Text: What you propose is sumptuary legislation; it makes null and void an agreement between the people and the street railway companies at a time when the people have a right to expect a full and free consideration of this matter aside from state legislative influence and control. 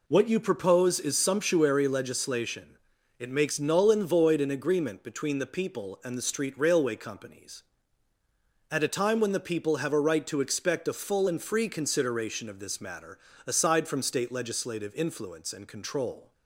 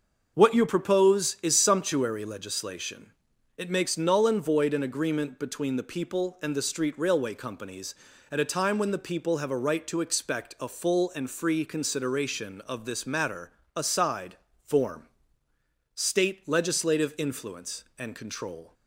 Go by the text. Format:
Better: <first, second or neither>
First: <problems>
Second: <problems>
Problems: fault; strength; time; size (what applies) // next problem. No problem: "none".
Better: first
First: pauses between "matter" and "aside"; slight; at 13.1 s; 0.30 s long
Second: starts louder than the rest; until 1.3 s; 6.5 dB // pauses between "matter" and "aside"; slight; at 13.5 s; 0.24 s long // says "form" for "from"; at 14.6 s